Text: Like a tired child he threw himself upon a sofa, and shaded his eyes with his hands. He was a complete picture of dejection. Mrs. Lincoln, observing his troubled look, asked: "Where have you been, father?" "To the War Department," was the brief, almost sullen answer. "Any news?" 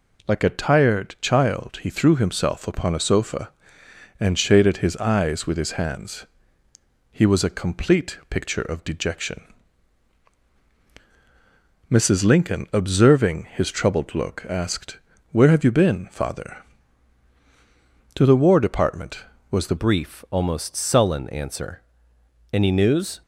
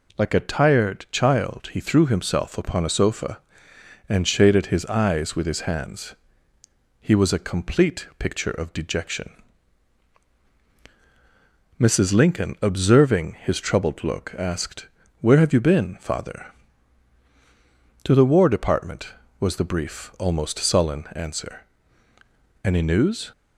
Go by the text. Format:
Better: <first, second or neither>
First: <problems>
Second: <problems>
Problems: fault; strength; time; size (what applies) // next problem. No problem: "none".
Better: second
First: changes voice at "brief"; from 19.7 s on; 3.5 s long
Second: none